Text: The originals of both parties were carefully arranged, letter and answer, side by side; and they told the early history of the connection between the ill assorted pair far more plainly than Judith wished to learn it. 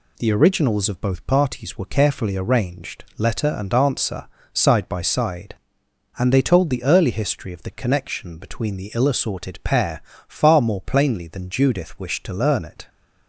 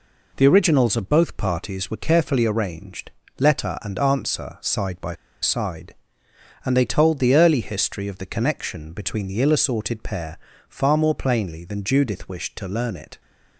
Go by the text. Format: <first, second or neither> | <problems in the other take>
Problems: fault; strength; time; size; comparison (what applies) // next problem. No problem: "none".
first | pauses between "by" and "side"; slight; at 5.1 s; 0.28 s long // pauses between "pair" and "far"; slight; at 10.3 s; 0.32 s long; slight in the first